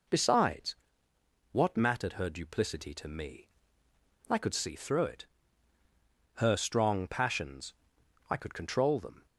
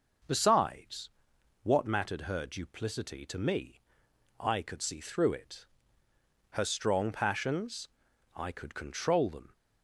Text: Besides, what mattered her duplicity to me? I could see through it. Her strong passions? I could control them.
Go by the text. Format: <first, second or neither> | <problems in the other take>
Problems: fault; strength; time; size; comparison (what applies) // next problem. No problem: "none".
neither | none